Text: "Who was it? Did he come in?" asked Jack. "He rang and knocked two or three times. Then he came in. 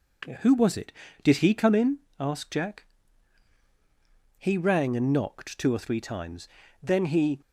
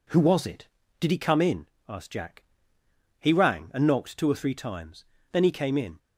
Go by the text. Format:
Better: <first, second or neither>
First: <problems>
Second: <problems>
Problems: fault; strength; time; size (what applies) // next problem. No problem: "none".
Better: second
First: stops before "came in"; at 7.4 s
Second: none